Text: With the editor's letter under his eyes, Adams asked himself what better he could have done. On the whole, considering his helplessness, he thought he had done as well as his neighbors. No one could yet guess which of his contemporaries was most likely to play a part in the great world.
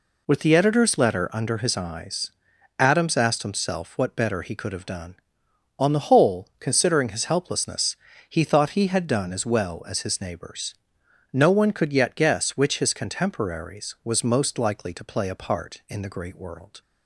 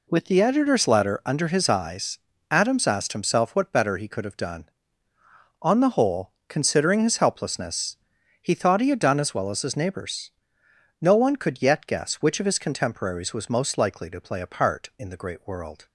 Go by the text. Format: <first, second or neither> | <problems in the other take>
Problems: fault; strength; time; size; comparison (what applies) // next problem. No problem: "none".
second | skips "of"; at 12.7 s